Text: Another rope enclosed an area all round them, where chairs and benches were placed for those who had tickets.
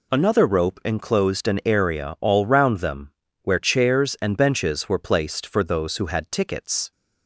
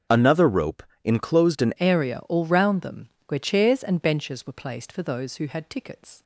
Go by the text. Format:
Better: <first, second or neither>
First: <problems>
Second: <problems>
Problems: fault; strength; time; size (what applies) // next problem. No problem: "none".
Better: first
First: none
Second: starts louder than the rest; strong; until 1.3 s; 7.5 dB // pauses between "rope" and "enclosed"; slight; at 0.8 s; 0.20 s long // changes voice at "area"; from 1.8 s on; 4.4 s long